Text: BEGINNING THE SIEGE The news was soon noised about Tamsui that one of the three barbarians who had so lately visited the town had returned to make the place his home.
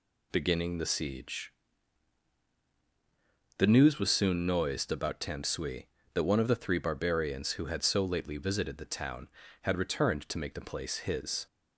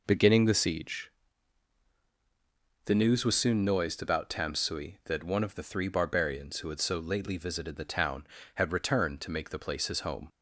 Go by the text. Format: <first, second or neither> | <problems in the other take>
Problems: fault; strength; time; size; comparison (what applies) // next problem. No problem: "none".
second | pauses between "SIEGE" and "The"; strong; at 1.5 s; 2.0 s long; strong in the second // stops before "home"; at 11.4 s